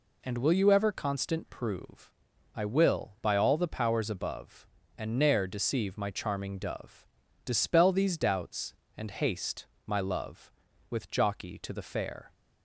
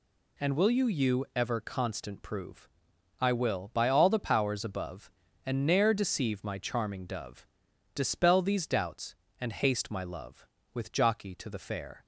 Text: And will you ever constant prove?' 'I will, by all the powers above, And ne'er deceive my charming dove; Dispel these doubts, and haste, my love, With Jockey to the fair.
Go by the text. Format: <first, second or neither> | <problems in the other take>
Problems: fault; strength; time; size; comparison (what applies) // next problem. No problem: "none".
first | says "you" twice; at 0.8 s